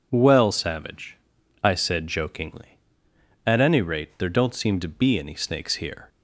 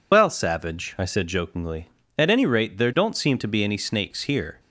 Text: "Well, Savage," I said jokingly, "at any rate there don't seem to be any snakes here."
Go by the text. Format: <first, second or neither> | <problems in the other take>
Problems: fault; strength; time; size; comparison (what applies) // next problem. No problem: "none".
first | loses the start of "Well"; at 0.1 s; 60 ms